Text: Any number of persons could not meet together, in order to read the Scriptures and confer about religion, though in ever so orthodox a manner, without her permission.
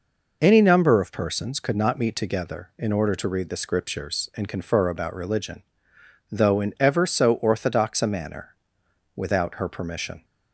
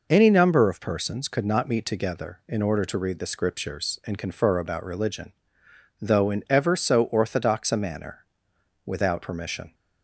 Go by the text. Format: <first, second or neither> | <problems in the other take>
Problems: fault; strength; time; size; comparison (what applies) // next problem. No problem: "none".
first | skips "her"; at 9.2 s